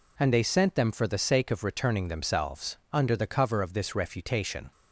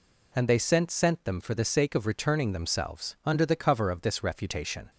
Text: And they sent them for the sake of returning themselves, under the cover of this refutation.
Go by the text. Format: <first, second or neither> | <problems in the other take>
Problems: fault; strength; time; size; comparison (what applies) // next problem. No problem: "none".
first | says "sent" twice; at 0.9 s